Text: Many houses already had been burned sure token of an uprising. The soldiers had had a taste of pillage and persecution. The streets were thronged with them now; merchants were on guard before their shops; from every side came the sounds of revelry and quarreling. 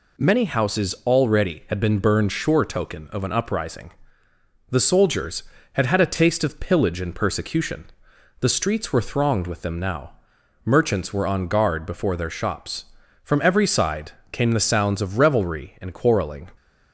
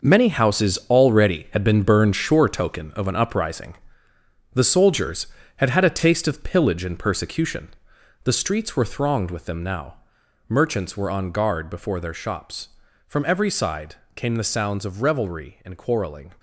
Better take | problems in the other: first | gets quieter; strong; throughout; 11 dB // pauses between "side" and "came"; slight; at 13.9 s; 0.18 s long; slight in the first

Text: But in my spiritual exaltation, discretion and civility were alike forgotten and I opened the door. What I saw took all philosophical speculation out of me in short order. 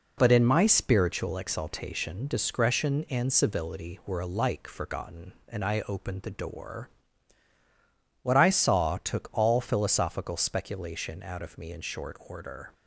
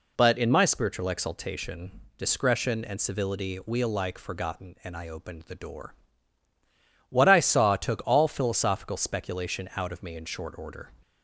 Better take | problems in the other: first | says "we" for "were"; at 3.6 s

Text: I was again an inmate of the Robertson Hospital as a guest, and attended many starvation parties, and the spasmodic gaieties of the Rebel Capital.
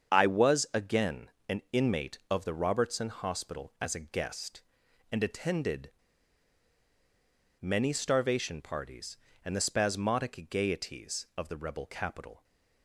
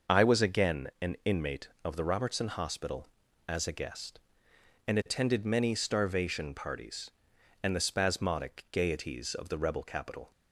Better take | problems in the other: second | starts louder than the rest; strong; until 1.2 s; 7.5 dB; noticeable in the second // pauses between "again" and "an"; slight; at 1.3 s; 0.18 s long // pauses between "attended" and "many"; strong; at 5.9 s; 1.6 s long

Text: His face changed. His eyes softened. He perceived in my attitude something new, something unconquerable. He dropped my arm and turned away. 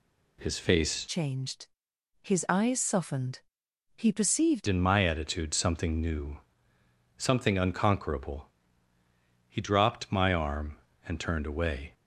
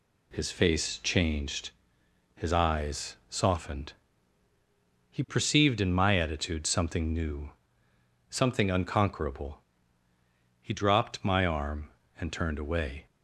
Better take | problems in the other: second | changes voice from "changed" to "perceived"; from 1.0 to 4.6 s; 3.6 s long

